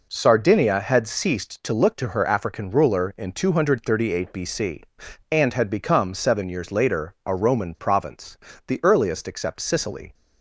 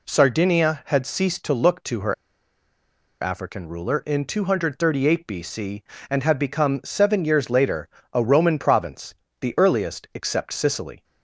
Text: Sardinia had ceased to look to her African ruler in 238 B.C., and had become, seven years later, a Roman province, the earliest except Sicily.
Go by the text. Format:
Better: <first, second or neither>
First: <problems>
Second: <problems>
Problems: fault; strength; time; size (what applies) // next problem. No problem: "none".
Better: first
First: none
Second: pauses between "her" and "African"; at 2.1 s; 1.0 s long